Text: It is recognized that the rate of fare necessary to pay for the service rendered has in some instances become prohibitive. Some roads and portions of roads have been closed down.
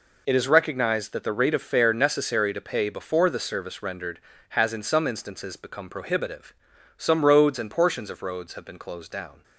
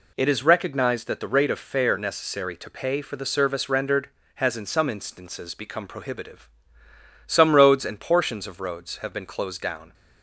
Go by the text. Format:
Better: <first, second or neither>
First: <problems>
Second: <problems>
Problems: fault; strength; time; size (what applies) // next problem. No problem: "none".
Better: second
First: says "before" for "for"; at 2.8 s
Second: none